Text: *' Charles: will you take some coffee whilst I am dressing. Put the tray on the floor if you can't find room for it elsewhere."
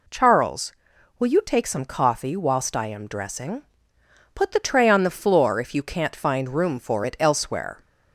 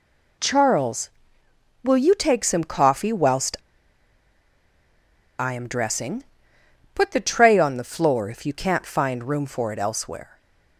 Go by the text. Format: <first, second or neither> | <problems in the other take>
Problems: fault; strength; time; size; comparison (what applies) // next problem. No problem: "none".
first | pauses between "whilst" and "I"; strong; at 3.5 s; 1.8 s long